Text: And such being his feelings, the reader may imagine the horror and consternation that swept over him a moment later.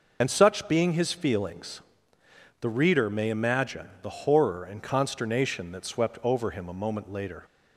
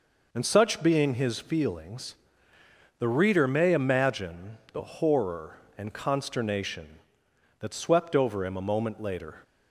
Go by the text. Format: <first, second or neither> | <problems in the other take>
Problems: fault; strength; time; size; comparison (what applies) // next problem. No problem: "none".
second | loses the start of "And"; at 0.2 s; 30 ms